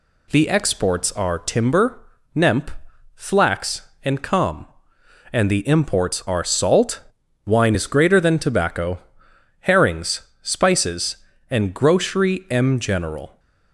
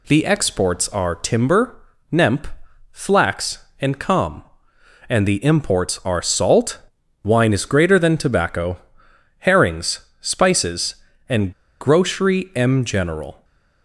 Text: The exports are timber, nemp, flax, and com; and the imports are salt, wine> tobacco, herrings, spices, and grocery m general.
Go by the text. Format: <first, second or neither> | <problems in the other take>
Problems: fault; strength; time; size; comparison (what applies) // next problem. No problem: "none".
first | pauses between "and" and "grocery"; slight; at 11.5 s; 0.28 s long